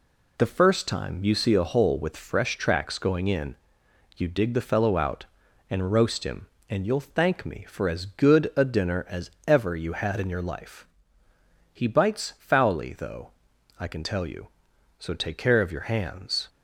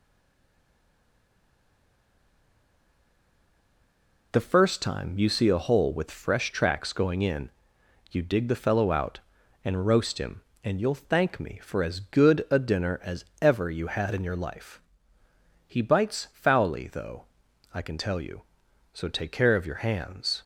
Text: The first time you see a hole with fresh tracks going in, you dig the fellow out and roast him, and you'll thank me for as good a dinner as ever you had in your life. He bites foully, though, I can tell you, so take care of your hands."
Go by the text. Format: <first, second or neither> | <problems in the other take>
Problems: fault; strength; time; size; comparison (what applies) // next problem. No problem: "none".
first | stays silent before the first word; strong; until 4.3 s; 4.3 s long // pauses between "as" and "ever"; slight; at 13.2 s; 0.16 s long; slight in the first